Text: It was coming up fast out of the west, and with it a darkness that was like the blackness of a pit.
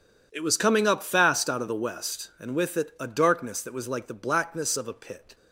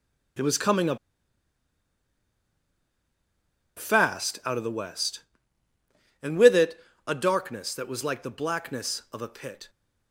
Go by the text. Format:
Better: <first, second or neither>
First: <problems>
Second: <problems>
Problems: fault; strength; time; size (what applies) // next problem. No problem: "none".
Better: first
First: none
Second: starts louder than the rest; strong; until 4.1 s; 9.5 dB // pauses between "up" and "fast"; strong; at 0.9 s; 2.7 s long // pauses between "it" and "a"; slight; at 6.7 s; 0.30 s long